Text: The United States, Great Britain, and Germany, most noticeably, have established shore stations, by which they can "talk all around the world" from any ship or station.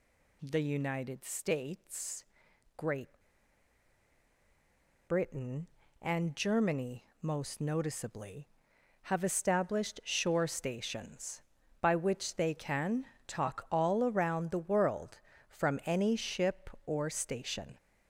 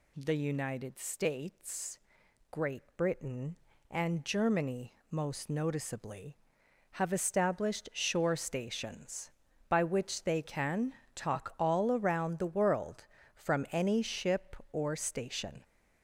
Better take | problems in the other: second | pauses between "Great" and "Britain"; strong; at 3.0 s; 1.9 s long // pauses between "can" and "talk"; slight; at 13.0 s; 0.20 s long; slight in the second

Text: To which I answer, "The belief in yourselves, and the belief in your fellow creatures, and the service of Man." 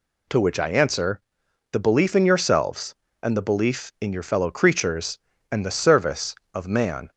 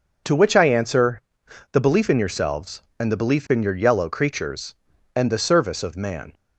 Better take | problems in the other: first | says "yellow" for "fellow"; at 3.7 s

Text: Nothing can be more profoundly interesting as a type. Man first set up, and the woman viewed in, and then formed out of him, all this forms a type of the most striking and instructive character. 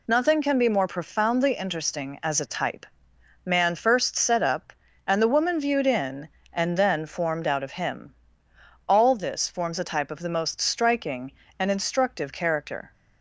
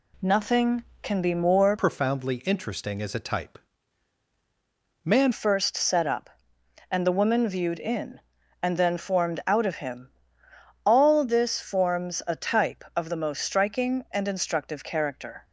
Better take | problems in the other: first | changes voice from "profoundly" to "Man"; from 1.7 to 5.3 s; 3.6 s long

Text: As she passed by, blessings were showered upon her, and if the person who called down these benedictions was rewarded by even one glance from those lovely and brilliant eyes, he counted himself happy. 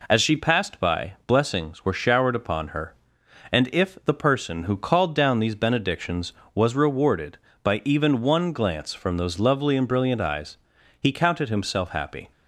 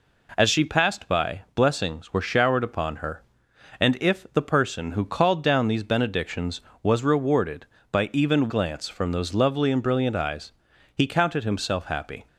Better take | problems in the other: first | skips "one"; at 8.4 s

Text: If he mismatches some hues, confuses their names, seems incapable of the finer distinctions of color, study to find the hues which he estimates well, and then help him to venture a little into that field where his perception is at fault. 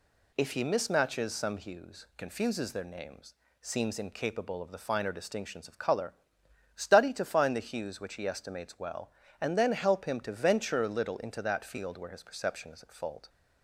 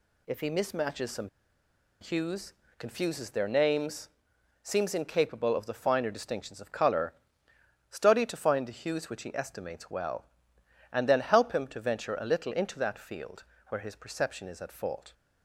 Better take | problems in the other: first | pauses between "some" and "hues"; noticeable; at 1.2 s; 0.73 s long // pauses between "field" and "where"; slight; at 13.4 s; 0.26 s long

